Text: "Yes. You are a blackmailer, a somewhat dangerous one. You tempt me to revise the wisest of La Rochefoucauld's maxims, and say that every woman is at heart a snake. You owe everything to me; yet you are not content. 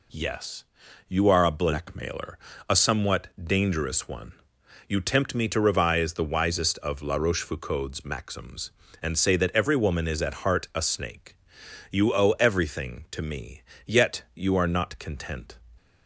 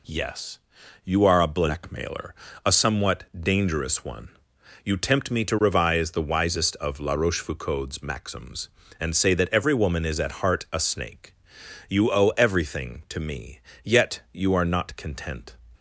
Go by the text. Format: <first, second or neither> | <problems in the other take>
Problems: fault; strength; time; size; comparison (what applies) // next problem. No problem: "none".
neither | none